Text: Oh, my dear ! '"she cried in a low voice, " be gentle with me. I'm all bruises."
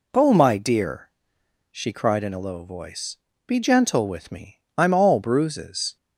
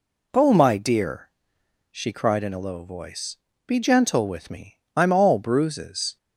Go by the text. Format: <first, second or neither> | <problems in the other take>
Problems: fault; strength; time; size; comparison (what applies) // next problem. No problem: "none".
neither | none